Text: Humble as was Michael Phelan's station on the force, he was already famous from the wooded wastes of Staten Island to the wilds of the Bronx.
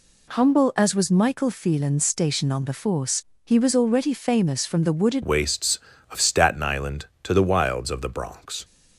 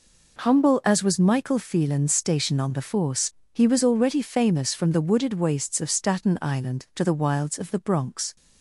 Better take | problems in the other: second | changes voice at "wastes"; from 5.2 s on; 3.4 s long

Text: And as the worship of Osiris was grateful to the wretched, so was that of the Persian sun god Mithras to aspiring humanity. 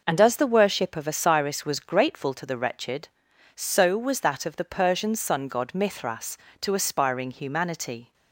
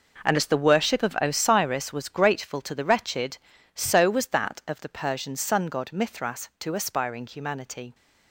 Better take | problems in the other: first | gets quieter; strong; throughout; 12 dB

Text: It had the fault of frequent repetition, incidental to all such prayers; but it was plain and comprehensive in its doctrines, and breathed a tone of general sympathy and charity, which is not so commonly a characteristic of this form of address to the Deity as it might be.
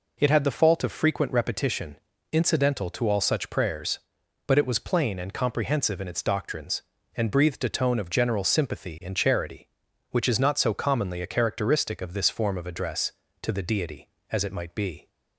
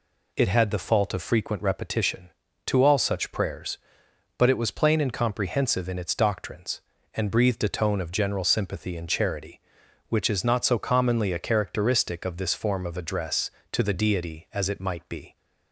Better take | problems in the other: first | skips "incidental"; at 2.4 s

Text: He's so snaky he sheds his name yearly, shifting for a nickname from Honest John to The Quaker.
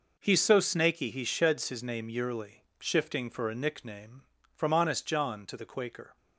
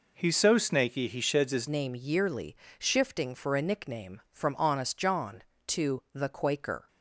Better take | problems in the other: first | changes voice at "name"; from 1.6 s on; 5.2 s long

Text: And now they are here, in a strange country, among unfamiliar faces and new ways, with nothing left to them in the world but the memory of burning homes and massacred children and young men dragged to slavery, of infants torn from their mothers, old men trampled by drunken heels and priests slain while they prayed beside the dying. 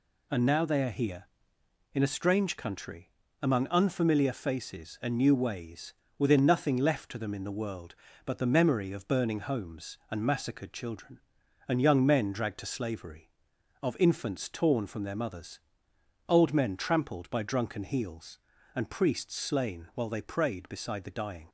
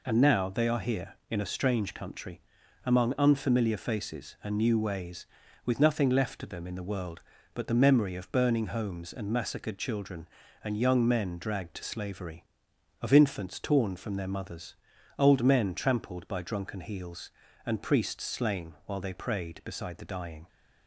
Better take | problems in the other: second | says "within" for "with"; at 6.1 s

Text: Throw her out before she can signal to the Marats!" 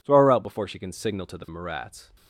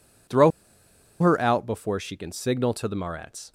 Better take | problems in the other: first | pauses between "Throw" and "her"; noticeable; at 0.5 s; 0.70 s long

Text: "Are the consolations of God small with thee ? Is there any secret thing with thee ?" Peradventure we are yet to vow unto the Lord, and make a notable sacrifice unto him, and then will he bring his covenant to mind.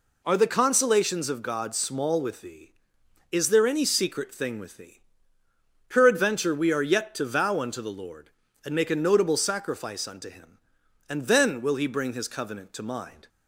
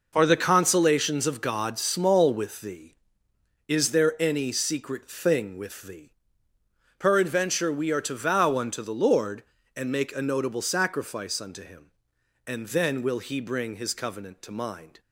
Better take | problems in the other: first | skips "yet"; at 8.0 s

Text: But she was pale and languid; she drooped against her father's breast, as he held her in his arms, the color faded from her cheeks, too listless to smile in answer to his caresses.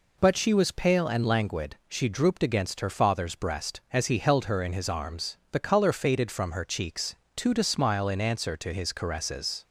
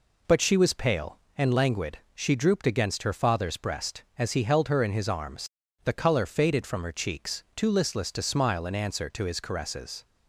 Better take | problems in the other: second | skips "listless"; at 7.5 s

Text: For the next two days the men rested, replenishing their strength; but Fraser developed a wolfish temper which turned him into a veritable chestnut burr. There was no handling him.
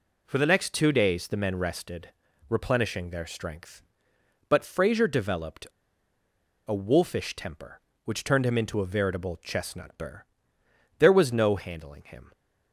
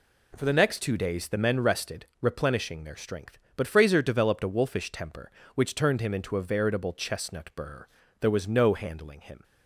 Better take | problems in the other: second | pauses between "developed" and "a"; at 5.6 s; 0.99 s long

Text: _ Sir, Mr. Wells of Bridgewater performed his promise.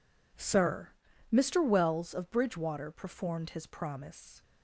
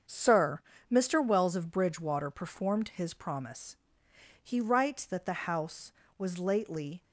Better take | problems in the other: first | starts louder than the rest; until 1.3 s; 7 dB // goes on to say "He writes that the house was lately"; strong; from 4.4 s on; 2.6 s long

